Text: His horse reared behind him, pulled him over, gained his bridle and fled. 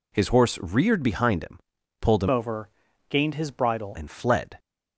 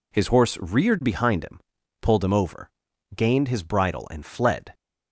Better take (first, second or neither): second